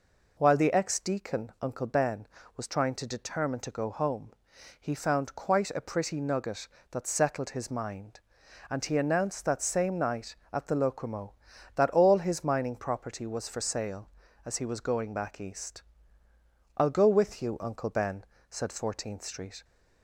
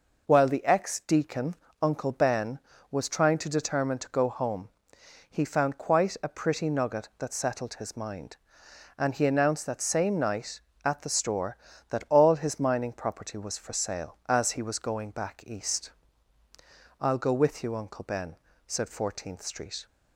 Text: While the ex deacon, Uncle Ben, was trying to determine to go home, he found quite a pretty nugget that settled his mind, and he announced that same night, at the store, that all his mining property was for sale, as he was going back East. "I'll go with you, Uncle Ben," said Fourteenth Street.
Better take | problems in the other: second | says "locomo" for "store"; at 10.7 s

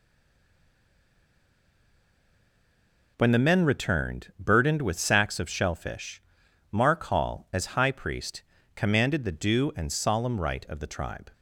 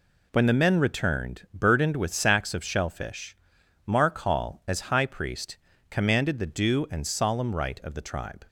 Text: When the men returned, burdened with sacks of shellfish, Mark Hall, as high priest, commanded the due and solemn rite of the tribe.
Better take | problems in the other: second | stays silent before the first word; strong; until 3.1 s; 3.1 s long

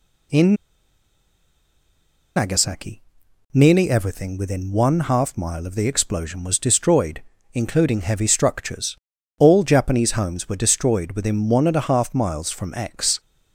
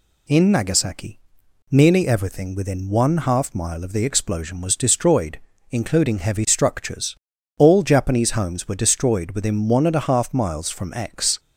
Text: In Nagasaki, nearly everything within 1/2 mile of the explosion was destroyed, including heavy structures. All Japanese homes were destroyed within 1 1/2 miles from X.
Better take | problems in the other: second | pauses between "In" and "Nagasaki"; strong; at 0.5 s; 1.8 s long

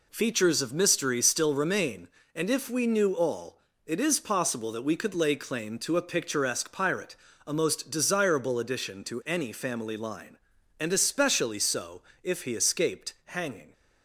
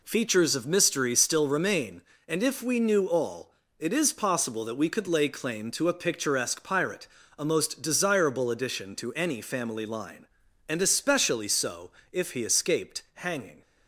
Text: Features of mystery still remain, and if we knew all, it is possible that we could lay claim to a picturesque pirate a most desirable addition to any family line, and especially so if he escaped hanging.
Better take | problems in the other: neither | pauses between "pirate" and "a"; slight; the same in both // pauses between "so" and "if"; slight; the same in both

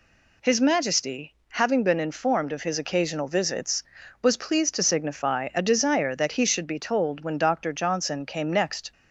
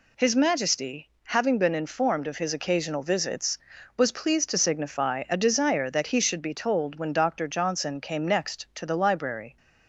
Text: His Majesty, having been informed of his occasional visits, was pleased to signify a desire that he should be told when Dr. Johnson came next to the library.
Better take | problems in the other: second | stops before "to the library"; at 8.9 s

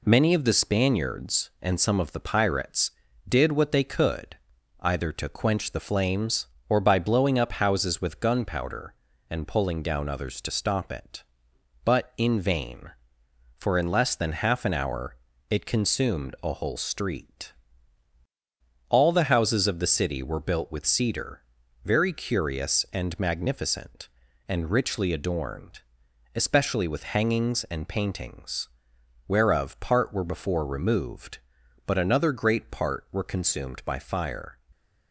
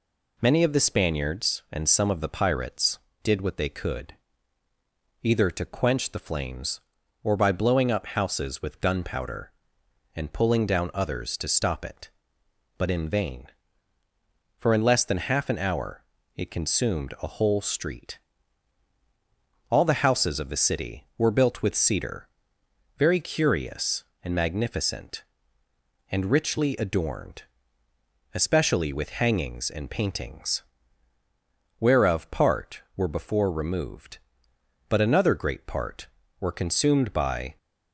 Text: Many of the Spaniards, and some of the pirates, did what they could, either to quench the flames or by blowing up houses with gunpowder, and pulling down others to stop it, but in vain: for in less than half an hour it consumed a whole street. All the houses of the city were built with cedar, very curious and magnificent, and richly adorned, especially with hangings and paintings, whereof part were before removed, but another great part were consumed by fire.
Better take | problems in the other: first | pauses between "hour" and "it"; slight; at 16.0 s; 0.32 s long; slight in the first // stops before "fire"; at 37.5 s

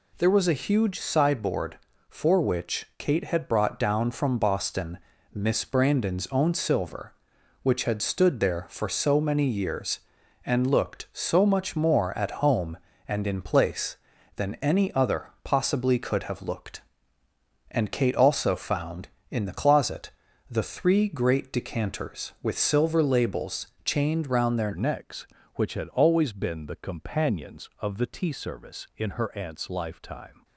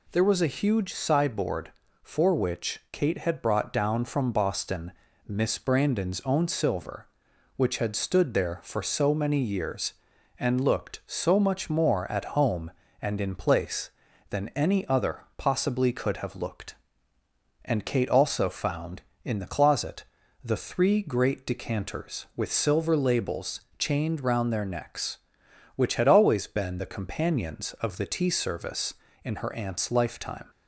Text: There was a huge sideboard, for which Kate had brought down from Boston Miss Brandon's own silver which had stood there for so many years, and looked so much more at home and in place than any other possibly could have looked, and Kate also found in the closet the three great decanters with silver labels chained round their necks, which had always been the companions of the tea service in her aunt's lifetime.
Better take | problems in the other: second | pauses between "Boston" and "Miss"; slight; at 4.9 s; 0.36 s long; slight in the second // pauses between "closet" and "the"; at 20.0 s; 0.40 s long; also in the second // pauses between "labels" and "chained"; slight; at 23.6 s; 0.18 s long; slight in the second // changes voice at "necks"; from 24.7 s on; 5.7 s long

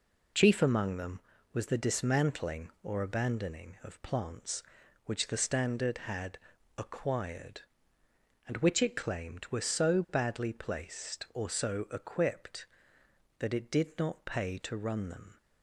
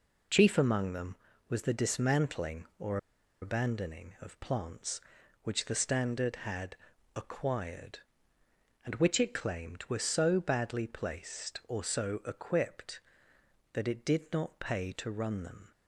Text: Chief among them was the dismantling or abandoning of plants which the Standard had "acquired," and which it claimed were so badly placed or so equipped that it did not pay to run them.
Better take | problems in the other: first | pauses between "or" and "abandoning"; at 2.9 s; 0.44 s long // pauses between "had" and "acquired"; at 6.7 s; 0.40 s long; also in the first

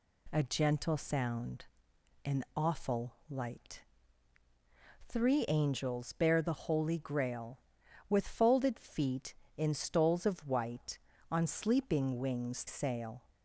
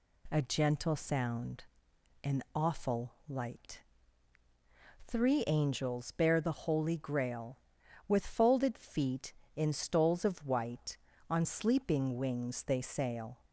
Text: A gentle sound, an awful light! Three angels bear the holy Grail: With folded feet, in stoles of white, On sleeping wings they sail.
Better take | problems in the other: second | pauses between "awful" and "light"; slight; at 3.1 s; 0.16 s long; slight in the second // skips "they"; at 12.6 s

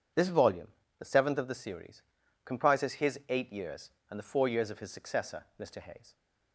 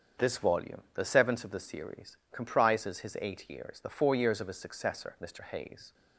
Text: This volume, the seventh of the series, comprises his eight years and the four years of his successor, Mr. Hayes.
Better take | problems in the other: first | starts louder than the rest; strong; until 1.3 s; 7 dB // skips "and"; at 3.7 s

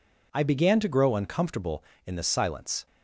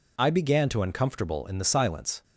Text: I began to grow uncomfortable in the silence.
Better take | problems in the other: first | skips "grow"; at 0.8 s

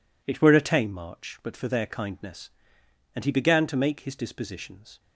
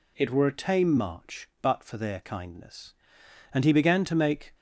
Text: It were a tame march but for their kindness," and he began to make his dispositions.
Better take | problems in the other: first | stops before "his dispositions"; at 4.5 s

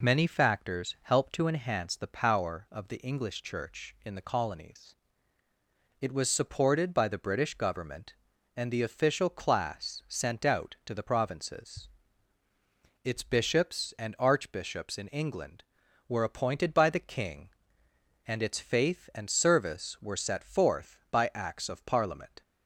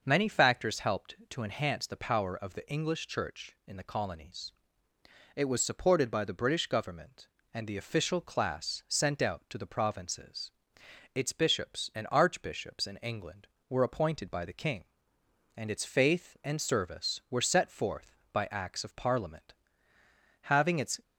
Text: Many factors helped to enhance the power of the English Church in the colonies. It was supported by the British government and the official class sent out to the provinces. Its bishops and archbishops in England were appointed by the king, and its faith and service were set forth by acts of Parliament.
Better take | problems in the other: first | starts louder than the rest; noticeable; until 1.0 s; 6 dB // goes on to say "Having its"; from 20.4 s on; 0.60 s long

